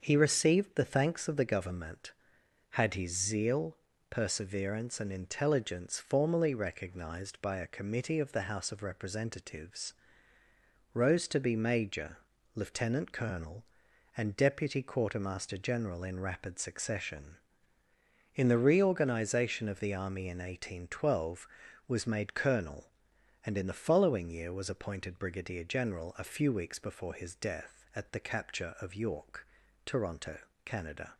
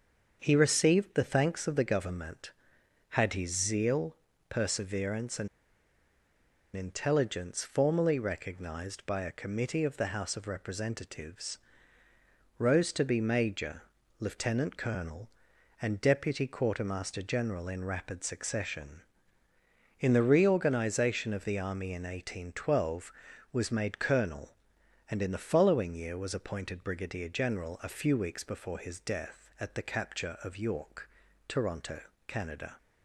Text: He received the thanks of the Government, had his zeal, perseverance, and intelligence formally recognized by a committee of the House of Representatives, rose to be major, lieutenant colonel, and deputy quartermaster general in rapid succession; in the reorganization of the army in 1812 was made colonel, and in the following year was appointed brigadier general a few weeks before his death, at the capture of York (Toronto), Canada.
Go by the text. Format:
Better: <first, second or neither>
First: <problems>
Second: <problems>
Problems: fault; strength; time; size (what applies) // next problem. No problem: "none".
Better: first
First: starts louder than the rest; until 1.0 s; 6.5 dB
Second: starts louder than the rest; until 1.4 s; 6.5 dB // pauses between "and" and "intelligence"; strong; at 5.4 s; 1.2 s long